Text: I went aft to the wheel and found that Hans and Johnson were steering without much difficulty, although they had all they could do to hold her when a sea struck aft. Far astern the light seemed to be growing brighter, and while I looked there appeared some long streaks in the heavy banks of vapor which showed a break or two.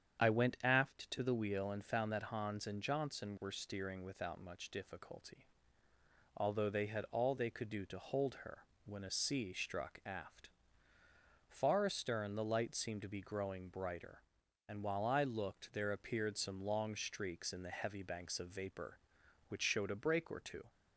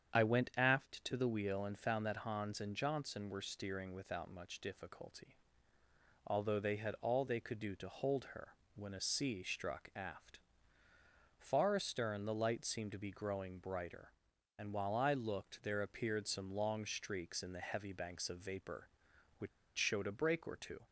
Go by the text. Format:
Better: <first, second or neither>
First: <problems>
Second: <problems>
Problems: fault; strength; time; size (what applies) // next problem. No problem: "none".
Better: first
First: starts louder than the rest; strong; until 1.2 s; 8.5 dB // pauses between "her" and "when"; slight; at 8.6 s; 0.22 s long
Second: starts louder than the rest; strong; until 1.2 s; 8.5 dB // pauses between "her" and "when"; slight; at 8.5 s; 0.22 s long // pauses between "which" and "showed"; slight; at 19.4 s; 0.28 s long